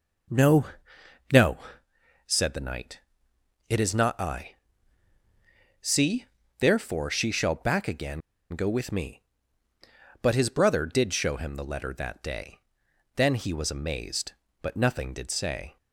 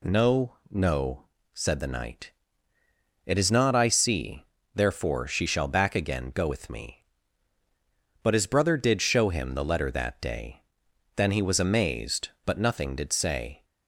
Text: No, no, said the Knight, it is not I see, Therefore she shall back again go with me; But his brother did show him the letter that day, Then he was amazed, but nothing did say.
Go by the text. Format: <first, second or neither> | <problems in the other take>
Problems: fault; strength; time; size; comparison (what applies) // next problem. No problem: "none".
second | pauses between "I" and "see"; strong; at 4.5 s; 1.2 s long // pauses between "again" and "go"; slight; at 8.2 s; 0.31 s long